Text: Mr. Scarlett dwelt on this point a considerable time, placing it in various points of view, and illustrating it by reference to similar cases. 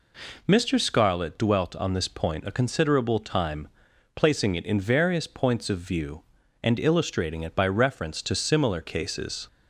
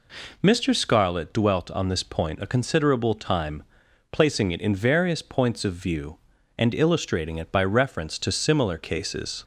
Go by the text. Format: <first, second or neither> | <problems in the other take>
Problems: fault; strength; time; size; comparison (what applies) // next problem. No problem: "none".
neither | none